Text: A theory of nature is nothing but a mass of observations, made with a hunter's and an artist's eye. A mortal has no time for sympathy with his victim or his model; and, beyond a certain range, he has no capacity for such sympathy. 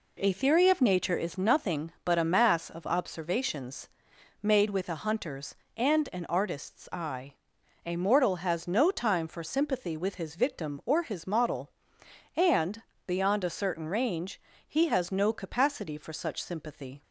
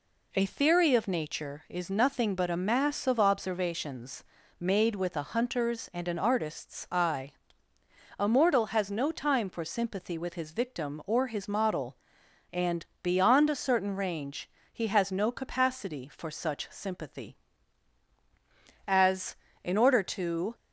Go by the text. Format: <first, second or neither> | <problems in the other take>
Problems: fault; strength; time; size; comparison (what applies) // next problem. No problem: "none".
first | goes on to say "As in order to"; strong; from 18.8 s on; 1.6 s long